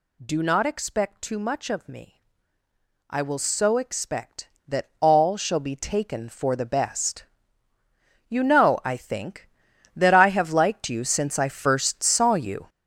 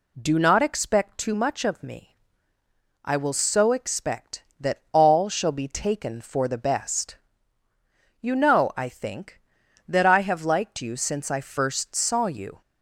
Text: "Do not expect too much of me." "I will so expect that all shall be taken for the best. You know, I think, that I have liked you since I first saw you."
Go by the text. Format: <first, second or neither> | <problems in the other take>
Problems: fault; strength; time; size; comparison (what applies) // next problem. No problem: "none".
second | gets louder; strong; throughout; 9.5 dB